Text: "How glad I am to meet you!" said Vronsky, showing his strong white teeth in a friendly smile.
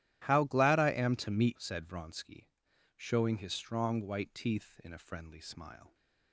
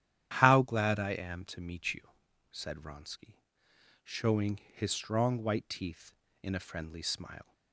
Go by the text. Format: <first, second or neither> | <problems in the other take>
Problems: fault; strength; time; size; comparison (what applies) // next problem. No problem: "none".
second | starts louder than the rest; strong; until 1.2 s; 12.5 dB; strong in the second // skips "you"; at 1.5 s